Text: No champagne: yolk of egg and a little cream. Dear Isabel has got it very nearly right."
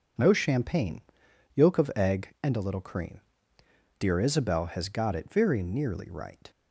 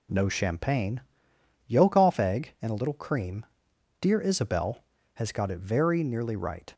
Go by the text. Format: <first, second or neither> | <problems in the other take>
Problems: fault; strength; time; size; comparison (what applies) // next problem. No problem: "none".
first | says "off" for "of"; at 1.9 s